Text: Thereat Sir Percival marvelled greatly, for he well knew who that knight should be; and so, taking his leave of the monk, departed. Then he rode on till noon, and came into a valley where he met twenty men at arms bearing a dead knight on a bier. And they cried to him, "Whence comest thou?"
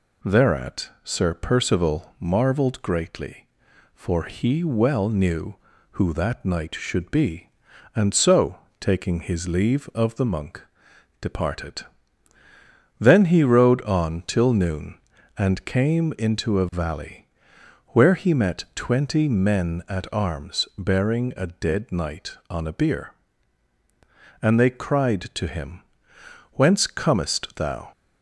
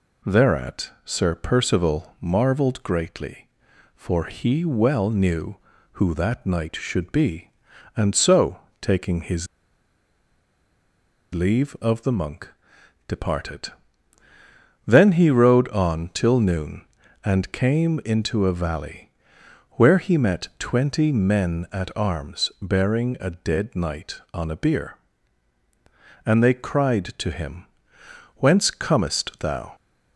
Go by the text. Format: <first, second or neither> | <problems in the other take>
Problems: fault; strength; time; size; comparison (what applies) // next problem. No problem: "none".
first | pauses between "his" and "leave"; strong; at 9.4 s; 1.8 s long // pauses between "valley" and "where"; noticeable; at 19.0 s; 0.62 s long; noticeable in the first